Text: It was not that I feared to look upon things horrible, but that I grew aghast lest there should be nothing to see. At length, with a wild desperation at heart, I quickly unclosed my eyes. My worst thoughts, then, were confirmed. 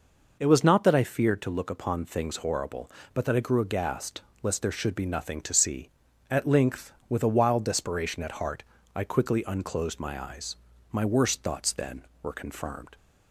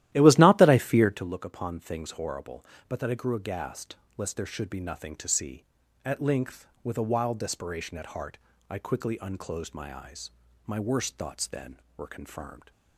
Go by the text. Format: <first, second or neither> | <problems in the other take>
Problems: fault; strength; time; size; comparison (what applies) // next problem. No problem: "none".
first | starts louder than the rest; strong; until 1.3 s; 14 dB // pauses between "aghast" and "lest"; slight; at 3.9 s; 0.20 s long; slight in the first